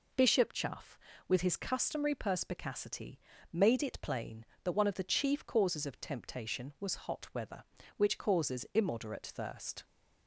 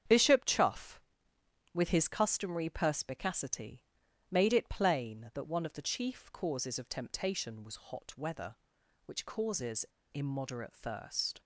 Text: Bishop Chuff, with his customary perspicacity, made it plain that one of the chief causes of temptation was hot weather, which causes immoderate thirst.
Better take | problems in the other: first | starts louder than the rest; strong; until 1.8 s; 8 dB // pauses between "causes" and "immoderate"; slight; at 9.8 s; 0.27 s long

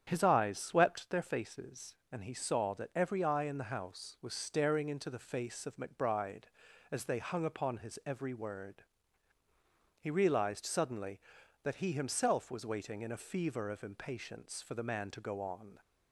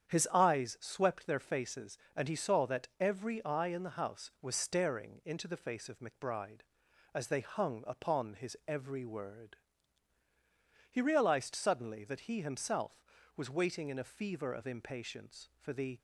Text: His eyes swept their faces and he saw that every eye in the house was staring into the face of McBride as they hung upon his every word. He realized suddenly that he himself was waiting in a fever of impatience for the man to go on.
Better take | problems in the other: first | starts louder than the rest; strong; until 1.1 s; 8.5 dB; strong in the first // stops before "man to go on"; at 15.9 s

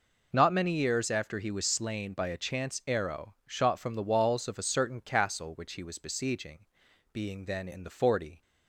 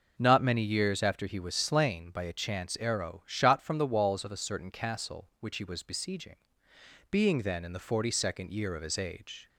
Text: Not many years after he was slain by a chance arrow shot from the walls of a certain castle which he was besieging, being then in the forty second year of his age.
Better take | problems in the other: second | stops before "second year of his age"; at 8.4 s

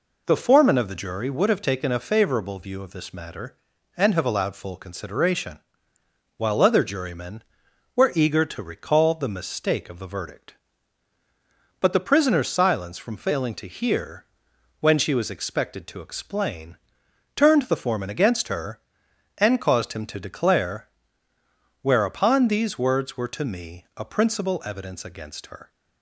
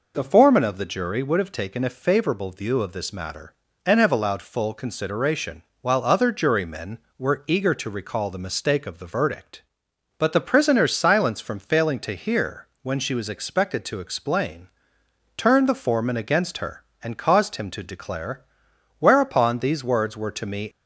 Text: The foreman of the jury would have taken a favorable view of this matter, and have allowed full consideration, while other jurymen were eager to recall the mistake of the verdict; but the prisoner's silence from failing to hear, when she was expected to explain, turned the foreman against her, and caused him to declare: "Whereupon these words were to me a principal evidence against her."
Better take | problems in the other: first | stops before "a principal evidence against her"; at 20.7 s

